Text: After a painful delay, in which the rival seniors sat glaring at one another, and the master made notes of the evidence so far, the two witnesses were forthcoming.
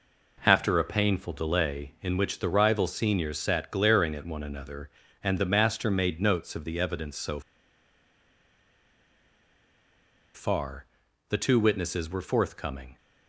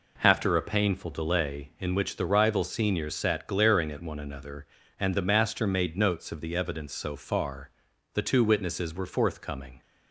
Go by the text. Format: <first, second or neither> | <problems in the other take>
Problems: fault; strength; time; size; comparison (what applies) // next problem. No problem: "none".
second | pauses between "so" and "far"; strong; at 7.4 s; 2.9 s long